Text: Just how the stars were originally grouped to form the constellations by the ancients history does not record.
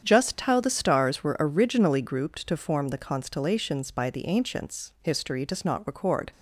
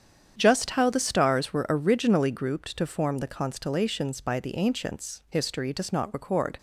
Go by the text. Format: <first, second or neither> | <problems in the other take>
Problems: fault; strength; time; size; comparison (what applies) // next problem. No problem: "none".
neither | starts louder than the rest; strong; the same in both